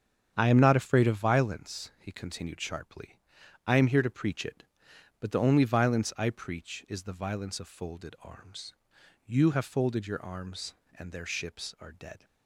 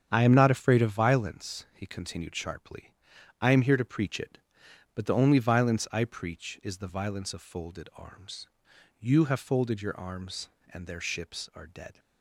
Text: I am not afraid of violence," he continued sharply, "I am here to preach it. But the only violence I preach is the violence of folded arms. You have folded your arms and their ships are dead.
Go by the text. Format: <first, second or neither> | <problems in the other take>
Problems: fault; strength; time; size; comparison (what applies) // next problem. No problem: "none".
neither | starts louder than the rest; strong; the same in both